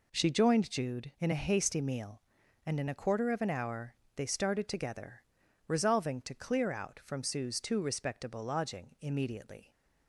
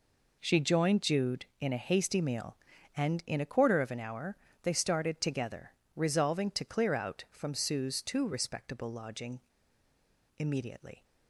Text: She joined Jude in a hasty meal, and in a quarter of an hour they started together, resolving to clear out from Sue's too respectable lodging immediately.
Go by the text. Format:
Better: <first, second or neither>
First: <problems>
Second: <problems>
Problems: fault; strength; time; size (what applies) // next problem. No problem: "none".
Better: first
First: pauses between "hour" and "they"; slight; at 3.9 s; 0.22 s long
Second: pauses between "hour" and "they"; slight; at 4.3 s; 0.26 s long // pauses between "lodging" and "immediately"; noticeable; at 9.4 s; 0.96 s long